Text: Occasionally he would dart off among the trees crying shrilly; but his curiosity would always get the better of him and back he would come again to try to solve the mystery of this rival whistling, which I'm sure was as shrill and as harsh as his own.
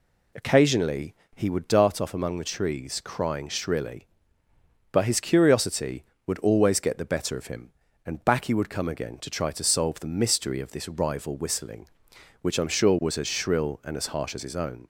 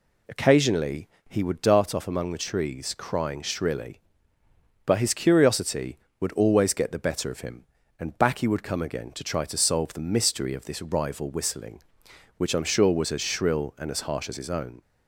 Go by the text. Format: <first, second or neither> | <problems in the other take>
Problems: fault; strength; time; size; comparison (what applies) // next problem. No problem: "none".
neither | pauses between "Occasionally" and "he"; slight; the same in both